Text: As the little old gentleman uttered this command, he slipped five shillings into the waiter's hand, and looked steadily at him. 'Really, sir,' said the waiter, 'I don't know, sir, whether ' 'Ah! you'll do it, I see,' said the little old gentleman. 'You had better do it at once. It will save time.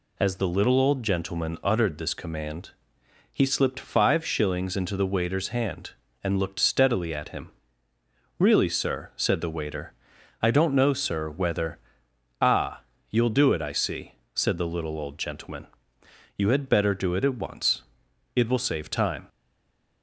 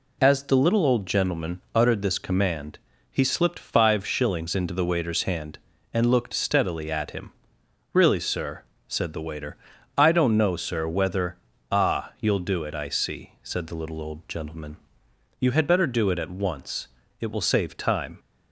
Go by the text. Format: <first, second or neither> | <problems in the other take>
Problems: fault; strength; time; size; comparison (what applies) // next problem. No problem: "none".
second | stays silent after the last word; slight; from 19.2 s on; 0.8 s long